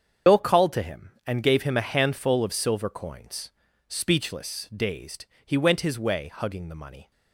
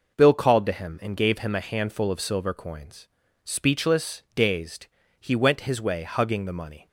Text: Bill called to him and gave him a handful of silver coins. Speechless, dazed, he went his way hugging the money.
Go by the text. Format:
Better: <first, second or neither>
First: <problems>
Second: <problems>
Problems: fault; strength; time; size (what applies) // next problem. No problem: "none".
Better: second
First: loses the start of "Bill"; at 0.2 s; 70 ms // starts louder than the rest; strong; until 1.4 s; 7 dB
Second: none